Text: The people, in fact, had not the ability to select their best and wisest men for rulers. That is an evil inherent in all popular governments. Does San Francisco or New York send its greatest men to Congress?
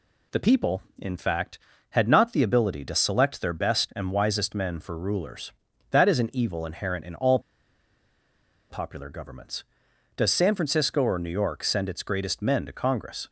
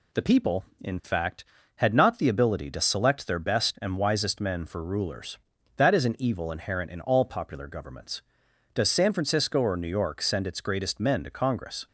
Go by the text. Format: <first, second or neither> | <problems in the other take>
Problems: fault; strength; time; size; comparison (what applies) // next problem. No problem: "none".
second | pauses between "all" and "popular"; strong; at 7.3 s; 1.3 s long